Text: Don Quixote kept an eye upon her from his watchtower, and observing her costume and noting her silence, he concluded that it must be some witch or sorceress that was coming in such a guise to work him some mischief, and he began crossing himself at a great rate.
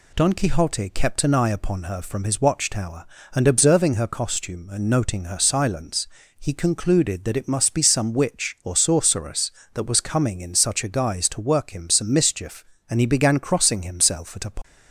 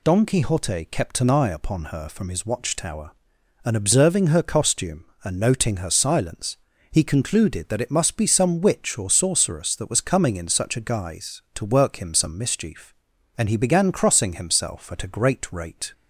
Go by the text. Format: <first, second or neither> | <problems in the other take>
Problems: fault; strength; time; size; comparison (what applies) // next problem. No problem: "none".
second | stops before "great rate"; at 14.6 s